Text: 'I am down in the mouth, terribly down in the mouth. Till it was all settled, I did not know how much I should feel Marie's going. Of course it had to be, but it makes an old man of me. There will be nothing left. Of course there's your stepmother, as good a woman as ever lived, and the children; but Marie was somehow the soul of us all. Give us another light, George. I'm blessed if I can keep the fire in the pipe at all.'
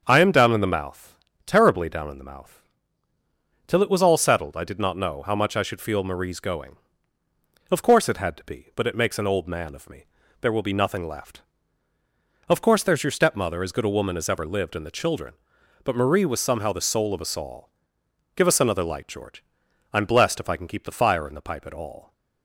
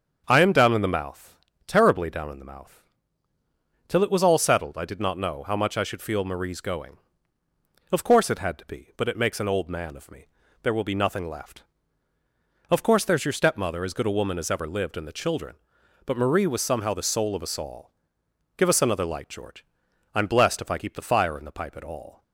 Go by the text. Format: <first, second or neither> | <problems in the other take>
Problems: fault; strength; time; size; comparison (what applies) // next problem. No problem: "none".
first | starts louder than the rest; strong; until 1.2 s; 7 dB; strong in the first // skips "can"; at 20.7 s